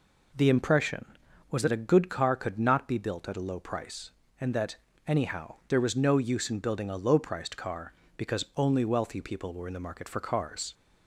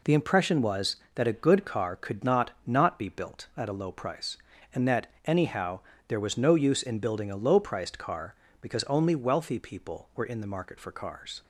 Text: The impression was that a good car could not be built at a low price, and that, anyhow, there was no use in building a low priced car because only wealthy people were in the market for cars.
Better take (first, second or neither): first